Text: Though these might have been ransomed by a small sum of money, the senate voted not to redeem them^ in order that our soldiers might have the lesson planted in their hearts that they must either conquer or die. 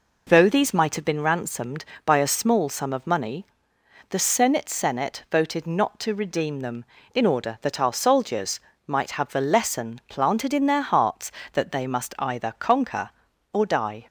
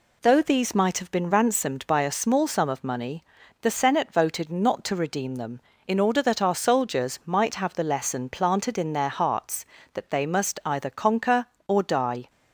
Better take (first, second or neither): second